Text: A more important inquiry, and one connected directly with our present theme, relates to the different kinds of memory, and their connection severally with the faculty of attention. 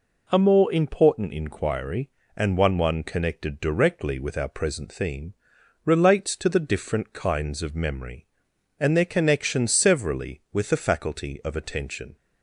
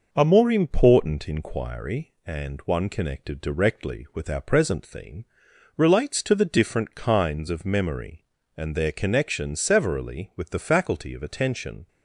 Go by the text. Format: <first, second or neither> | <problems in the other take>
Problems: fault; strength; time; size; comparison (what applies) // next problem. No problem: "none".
second | says "one" twice; at 2.7 s